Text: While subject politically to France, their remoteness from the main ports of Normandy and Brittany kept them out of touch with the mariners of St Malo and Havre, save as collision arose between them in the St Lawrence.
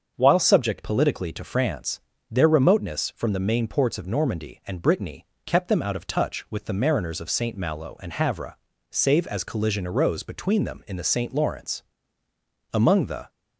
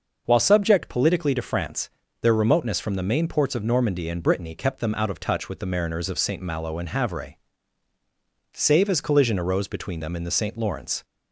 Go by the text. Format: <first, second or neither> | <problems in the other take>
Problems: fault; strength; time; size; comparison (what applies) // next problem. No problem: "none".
second | starts louder than the rest; until 1.1 s; 6.5 dB; noticeable in the second // pauses between "Brittany" and "kept"; slight; at 5.2 s; 0.18 s long // goes on to say "Among the"; from 12.7 s on; 0.58 s long